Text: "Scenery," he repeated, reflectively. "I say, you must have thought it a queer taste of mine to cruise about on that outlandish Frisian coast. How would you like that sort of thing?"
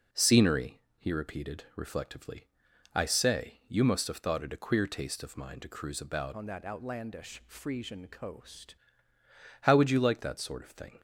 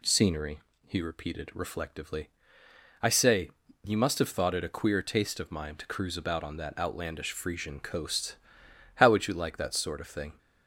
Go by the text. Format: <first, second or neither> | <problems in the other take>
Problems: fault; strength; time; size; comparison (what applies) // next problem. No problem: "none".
second | changes voice from "on" to "coast"; from 6.3 to 8.7 s; 2.4 s long